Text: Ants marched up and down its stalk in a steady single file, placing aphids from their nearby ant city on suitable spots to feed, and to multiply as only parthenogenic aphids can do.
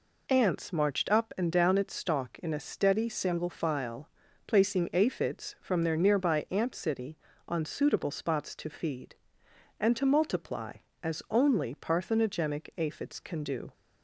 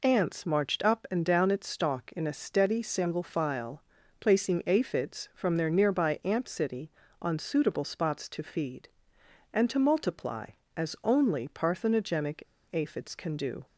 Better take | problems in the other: first | pauses between "parthenogenic" and "aphids"; slight; at 12.4 s; 0.30 s long

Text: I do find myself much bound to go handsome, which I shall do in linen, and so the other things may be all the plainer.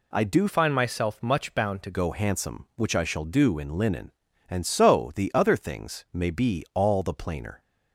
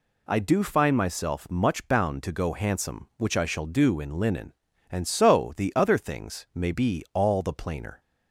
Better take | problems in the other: second | changes voice from "find" to "to"; from 0.4 to 1.9 s; 1.5 s long

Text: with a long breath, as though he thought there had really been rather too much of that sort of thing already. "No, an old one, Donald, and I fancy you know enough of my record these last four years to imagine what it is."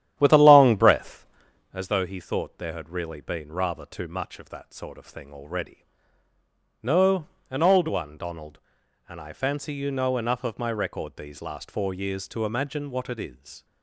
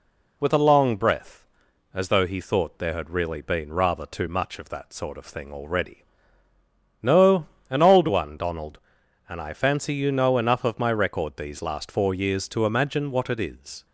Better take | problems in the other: second | starts louder than the rest; strong; until 1.8 s; 11 dB

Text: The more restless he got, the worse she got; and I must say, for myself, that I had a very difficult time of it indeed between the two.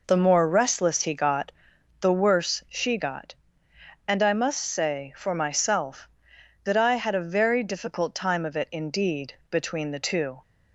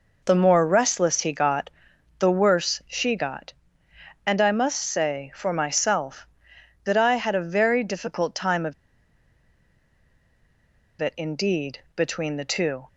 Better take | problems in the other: first | pauses between "of" and "it"; strong; at 8.7 s; 2.2 s long // pauses between "indeed" and "between"; slight; at 11.7 s; 0.18 s long; slight in the first

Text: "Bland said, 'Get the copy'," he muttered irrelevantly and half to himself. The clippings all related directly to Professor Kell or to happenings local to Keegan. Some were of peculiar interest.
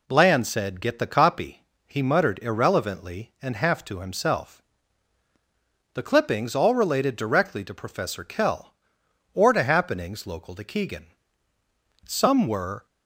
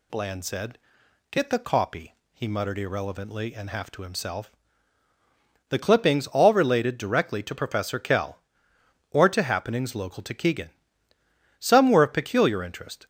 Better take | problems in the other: second | stops before "of peculiar interest"; at 12.8 s

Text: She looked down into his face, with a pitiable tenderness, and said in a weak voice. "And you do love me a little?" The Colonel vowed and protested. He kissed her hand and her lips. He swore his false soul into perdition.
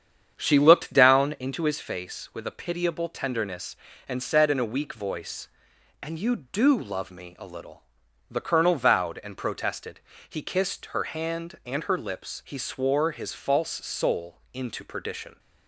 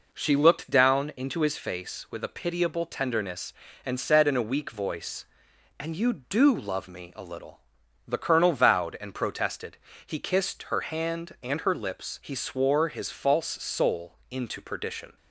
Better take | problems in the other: second | starts louder than the rest; strong; until 1.5 s; 8 dB

